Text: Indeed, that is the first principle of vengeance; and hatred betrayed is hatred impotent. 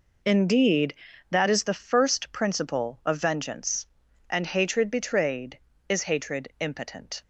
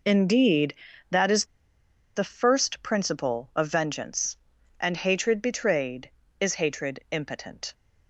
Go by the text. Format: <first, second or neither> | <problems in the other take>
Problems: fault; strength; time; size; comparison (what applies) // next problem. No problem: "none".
first | pauses between "is" and "the"; noticeable; at 1.4 s; 0.71 s long